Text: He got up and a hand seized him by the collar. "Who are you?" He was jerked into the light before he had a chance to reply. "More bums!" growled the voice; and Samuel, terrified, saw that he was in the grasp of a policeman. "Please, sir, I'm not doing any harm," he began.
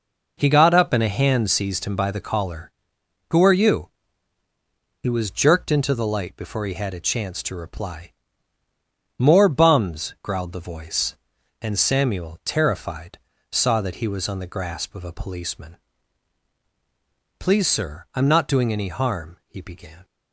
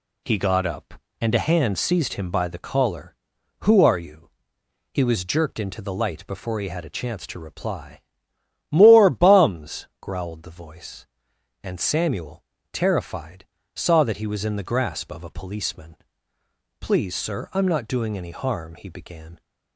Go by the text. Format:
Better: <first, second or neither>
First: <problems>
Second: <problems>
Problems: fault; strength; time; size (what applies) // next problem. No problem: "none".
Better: second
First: says "on" for "in"; at 14.2 s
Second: none